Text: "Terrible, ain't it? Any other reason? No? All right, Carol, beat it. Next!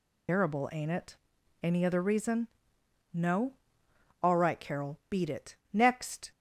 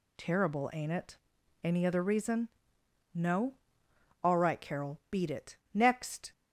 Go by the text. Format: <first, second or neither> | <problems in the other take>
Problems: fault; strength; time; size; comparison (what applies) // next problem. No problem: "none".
second | loses the start of "Terrible"; at 0.2 s; 120 ms